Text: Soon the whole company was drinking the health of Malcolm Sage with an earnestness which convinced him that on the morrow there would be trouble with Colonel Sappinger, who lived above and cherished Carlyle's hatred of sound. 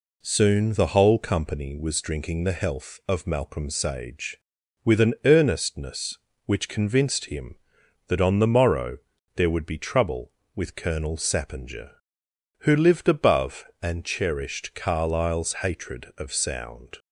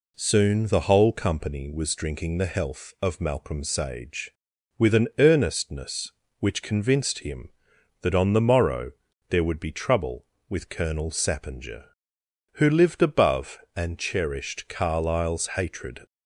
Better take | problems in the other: first | pauses between "morrow" and "there"; at 8.9 s; 0.38 s long; also in the first // stops before "of sound"; at 16.0 s

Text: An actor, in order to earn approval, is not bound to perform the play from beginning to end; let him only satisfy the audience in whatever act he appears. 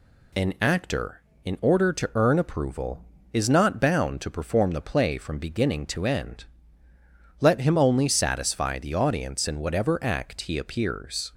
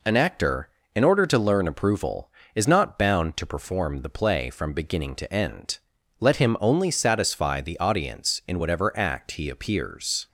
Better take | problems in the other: first | says "learn" for "earn"; at 1.3 s

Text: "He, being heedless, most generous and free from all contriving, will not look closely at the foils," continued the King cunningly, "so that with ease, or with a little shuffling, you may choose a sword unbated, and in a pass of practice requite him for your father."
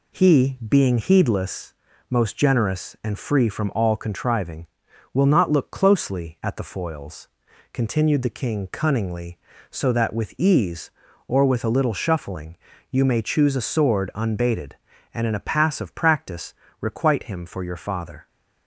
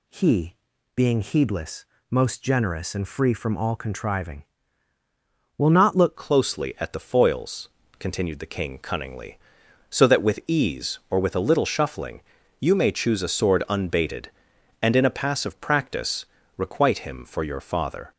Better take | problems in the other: first | changes voice at "closely"; from 6.1 s on; 12.0 s long // pauses between "practice" and "requite"; slight; at 16.2 s; 0.32 s long; slight in the first

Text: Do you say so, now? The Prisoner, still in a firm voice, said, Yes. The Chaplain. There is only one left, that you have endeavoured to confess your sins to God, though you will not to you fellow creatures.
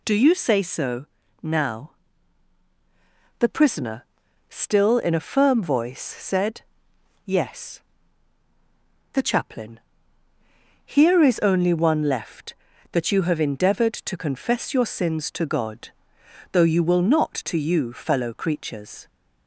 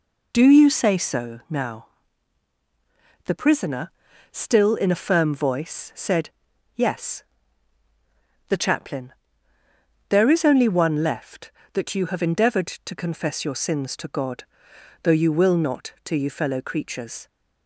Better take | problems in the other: second | says "Here" for "There"; at 10.8 s

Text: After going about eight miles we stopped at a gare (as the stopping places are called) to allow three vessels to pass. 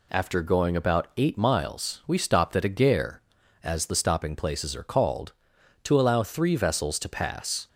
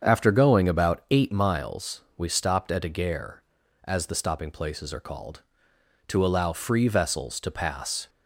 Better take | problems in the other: first | starts louder than the rest; strong; until 1.0 s; 7.5 dB // pauses between "miles" and "we"; slight; at 2.0 s; 0.16 s long // says "free" for "three"; at 6.5 s

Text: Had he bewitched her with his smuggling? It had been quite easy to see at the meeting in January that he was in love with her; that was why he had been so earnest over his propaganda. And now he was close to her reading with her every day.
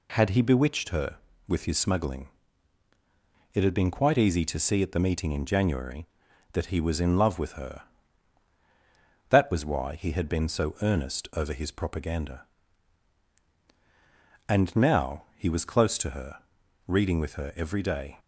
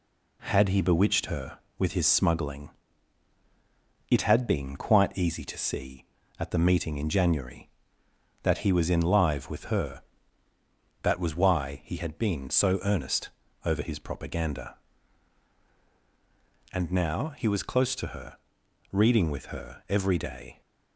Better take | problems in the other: first | says "live" for "love"; at 9.0 s // pauses between "earnest" and "over"; at 13.2 s; 0.38 s long // pauses between "her" and "reading"; noticeable; at 18.3 s; 0.54 s long; noticeable in the first

